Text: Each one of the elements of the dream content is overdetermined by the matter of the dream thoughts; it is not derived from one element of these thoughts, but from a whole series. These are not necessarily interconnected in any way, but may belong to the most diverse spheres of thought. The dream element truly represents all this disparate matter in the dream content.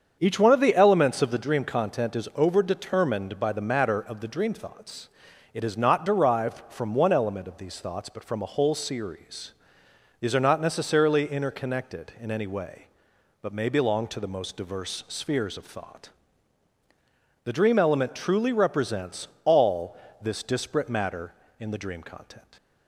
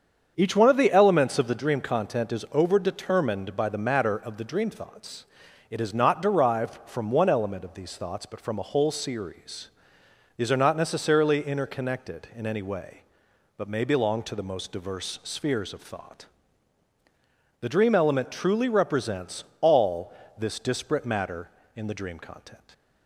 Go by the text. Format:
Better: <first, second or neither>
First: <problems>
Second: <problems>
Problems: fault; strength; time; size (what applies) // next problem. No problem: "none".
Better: neither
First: starts louder than the rest; strong; until 1.2 s; 7 dB // pauses between "represents" and "all"; slight; at 19.2 s; 0.16 s long // pauses between "all" and "this"; slight; at 19.9 s; 0.24 s long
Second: starts louder than the rest; strong; until 1.3 s; 7 dB // pauses between "represents" and "all"; slight; at 19.4 s; 0.16 s long // pauses between "all" and "this"; slight; at 20.1 s; 0.24 s long